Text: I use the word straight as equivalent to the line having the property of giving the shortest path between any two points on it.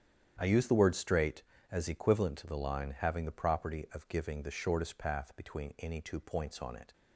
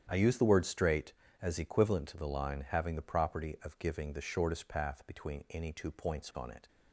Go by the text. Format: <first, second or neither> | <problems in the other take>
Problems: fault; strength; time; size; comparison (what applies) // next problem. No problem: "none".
neither | starts louder than the rest; strong; the same in both